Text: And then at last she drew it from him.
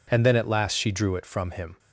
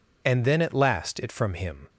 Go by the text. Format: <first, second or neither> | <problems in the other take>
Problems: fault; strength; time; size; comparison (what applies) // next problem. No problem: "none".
first | skips "she drew"; at 1.1 s